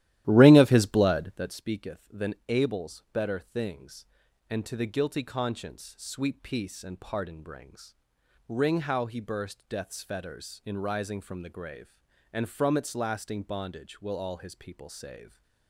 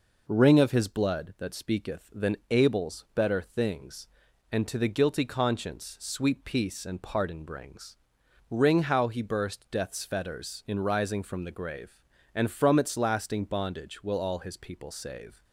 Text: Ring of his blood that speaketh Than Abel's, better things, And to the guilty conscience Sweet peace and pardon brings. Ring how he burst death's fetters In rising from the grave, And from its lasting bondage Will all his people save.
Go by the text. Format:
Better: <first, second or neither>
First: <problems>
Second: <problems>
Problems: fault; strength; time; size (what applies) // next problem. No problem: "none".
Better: second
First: starts louder than the rest; strong; until 1.6 s; 13.5 dB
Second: none